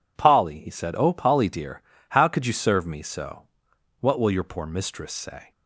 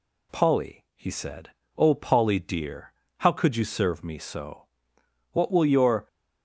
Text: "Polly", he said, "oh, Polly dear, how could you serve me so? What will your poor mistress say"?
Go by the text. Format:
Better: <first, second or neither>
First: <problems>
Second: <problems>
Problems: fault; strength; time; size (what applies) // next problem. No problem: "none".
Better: first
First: none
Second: stops before "poor mistress say"; at 6.0 s